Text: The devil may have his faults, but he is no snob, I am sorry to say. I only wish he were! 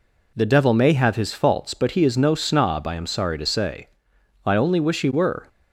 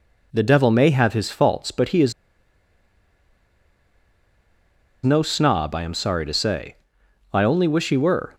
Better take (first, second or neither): first